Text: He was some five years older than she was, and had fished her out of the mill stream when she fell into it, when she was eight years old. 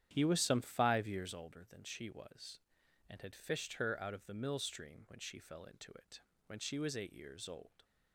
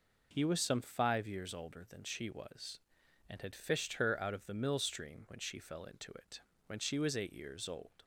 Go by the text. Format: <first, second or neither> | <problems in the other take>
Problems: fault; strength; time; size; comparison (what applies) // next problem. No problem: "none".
second | starts louder than the rest; strong; until 1.4 s; 10 dB